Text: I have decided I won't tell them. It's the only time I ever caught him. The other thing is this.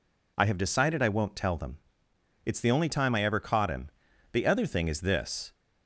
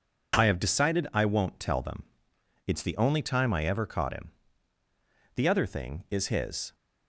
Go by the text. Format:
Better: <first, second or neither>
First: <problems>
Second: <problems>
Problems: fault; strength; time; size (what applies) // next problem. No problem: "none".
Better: first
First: none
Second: says "his" for "this"; at 6.2 s